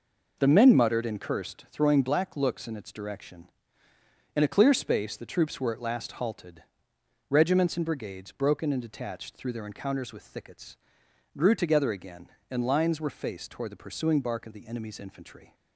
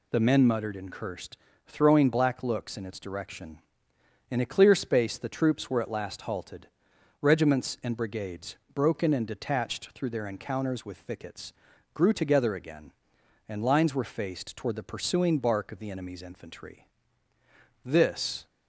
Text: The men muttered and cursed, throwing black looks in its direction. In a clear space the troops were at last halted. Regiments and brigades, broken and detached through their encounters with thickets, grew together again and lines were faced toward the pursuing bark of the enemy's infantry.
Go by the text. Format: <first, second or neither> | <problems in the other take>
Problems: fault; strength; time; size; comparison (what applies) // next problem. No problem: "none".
first | goes on to say "This"; noticeable; from 17.8 s on; 0.62 s long